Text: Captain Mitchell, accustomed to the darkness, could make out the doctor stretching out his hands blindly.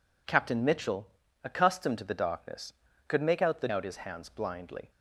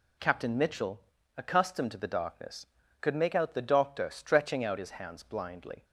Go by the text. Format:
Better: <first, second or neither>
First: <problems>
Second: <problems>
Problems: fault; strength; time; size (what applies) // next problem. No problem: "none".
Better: second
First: skips "doctor stretching"; at 3.6 s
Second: none